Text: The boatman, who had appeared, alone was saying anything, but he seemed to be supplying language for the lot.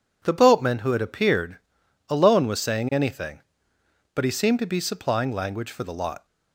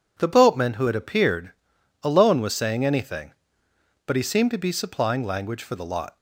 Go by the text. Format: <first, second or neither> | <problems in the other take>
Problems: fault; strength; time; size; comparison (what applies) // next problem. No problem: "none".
neither | none